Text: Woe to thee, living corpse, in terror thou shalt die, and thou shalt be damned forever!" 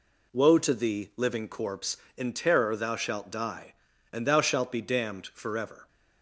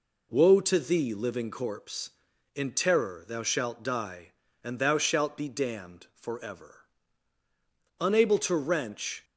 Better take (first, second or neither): first